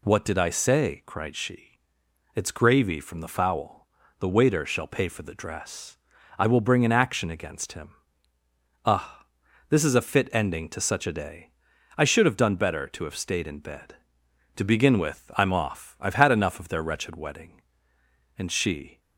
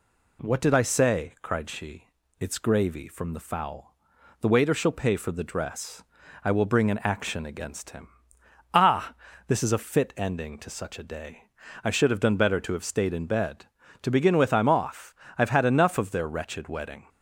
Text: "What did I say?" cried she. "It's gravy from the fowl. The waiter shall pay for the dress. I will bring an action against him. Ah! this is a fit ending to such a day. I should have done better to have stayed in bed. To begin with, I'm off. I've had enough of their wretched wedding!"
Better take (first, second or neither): second